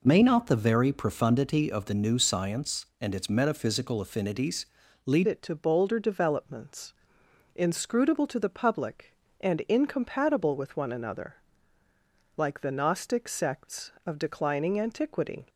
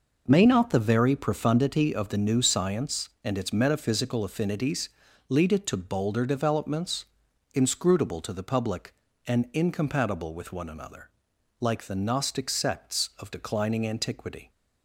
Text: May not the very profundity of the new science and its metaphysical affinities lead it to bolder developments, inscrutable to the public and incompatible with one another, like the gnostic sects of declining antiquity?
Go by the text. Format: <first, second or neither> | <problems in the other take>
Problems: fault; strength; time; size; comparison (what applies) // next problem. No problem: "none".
second | pauses between "affinities" and "lead"; at 4.6 s; 0.40 s long; also in the second // changes voice at "it"; from 5.2 s on; 10.2 s long